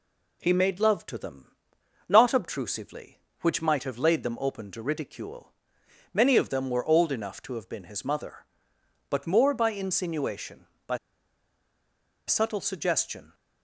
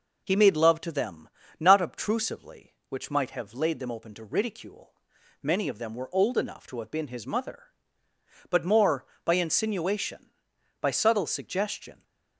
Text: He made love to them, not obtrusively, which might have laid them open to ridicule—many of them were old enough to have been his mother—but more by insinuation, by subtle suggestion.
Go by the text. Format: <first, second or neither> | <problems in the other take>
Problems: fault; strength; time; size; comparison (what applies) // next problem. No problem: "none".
second | pauses between "by" and "subtle"; strong; at 10.9 s; 1.3 s long